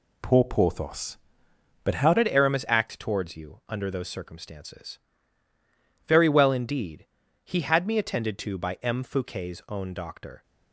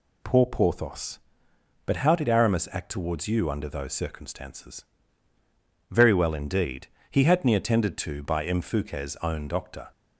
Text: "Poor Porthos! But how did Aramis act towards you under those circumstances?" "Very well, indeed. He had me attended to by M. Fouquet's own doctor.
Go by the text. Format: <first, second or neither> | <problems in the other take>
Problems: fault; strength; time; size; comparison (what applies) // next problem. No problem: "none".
second | changes voice at "did"; from 2.1 s on; 8.3 s long